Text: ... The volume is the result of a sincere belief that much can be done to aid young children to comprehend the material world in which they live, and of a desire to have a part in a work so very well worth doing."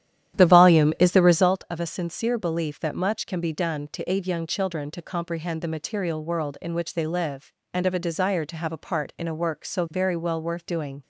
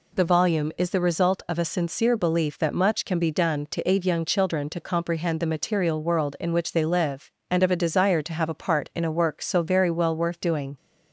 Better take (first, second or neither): second